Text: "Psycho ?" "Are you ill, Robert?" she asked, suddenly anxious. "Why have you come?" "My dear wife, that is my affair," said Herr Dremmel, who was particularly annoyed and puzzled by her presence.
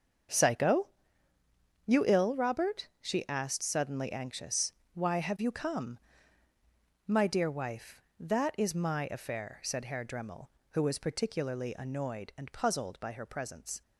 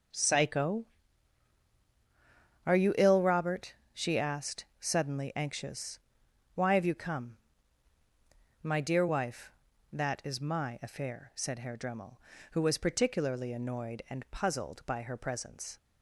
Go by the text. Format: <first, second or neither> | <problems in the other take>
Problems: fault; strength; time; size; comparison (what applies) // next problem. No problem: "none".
second | skips "Are"; at 1.8 s